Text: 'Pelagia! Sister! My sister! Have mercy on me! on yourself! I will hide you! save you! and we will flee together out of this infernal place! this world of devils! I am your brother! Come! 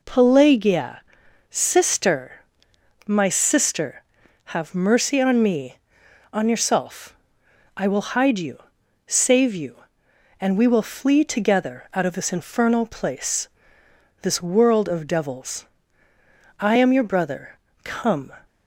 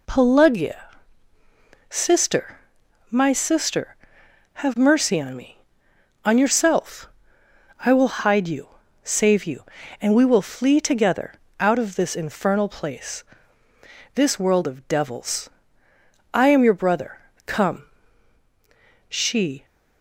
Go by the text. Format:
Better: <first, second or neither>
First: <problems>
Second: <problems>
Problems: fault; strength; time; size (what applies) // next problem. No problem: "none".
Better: first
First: none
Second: pauses between "together" and "out"; slight; at 11.3 s; 0.26 s long // goes on to say "She"; from 19.0 s on; 0.56 s long